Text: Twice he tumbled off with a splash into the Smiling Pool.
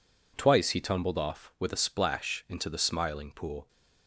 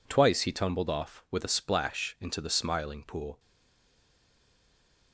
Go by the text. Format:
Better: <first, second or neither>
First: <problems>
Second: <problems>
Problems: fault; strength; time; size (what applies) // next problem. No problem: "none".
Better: first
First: none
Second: stays silent after the last word; noticeable; from 3.3 s on; 1.8 s long